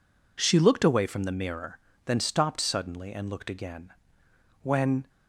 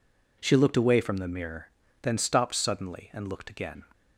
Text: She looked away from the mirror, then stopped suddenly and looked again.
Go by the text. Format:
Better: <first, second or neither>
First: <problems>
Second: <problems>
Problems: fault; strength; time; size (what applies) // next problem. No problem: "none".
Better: second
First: goes on to say "When"; slight; from 4.6 s on; 0.46 s long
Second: none